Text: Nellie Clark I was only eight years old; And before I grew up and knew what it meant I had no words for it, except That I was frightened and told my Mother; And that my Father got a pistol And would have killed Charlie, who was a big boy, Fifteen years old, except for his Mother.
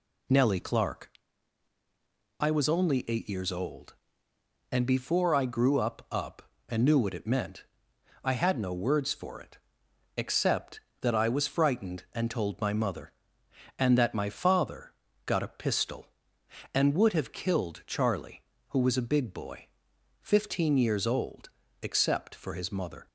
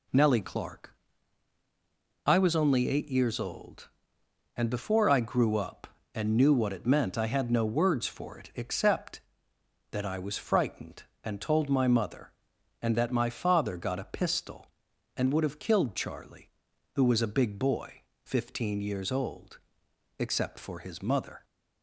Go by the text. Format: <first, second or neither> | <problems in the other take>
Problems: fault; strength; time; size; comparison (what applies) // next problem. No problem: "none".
second | pauses between "Clark" and "I"; strong; at 1.0 s; 1.3 s long; strong in the second // says "up" twice; at 6.1 s // pauses between "meant" and "I"; noticeable; at 7.6 s; 0.62 s long // pauses between "Father" and "got"; slight; at 14.9 s; 0.36 s long